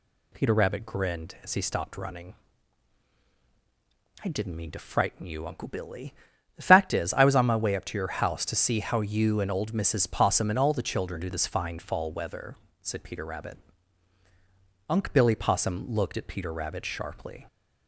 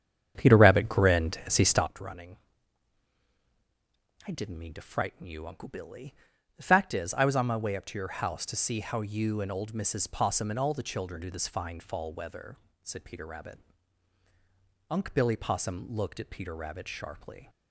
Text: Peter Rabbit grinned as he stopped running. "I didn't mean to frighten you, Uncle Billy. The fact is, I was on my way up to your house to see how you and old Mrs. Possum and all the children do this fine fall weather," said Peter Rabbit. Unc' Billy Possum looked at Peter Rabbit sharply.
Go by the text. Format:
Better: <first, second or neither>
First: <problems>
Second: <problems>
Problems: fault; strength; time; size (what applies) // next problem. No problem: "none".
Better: first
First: none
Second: starts louder than the rest; strong; until 1.9 s; 8.5 dB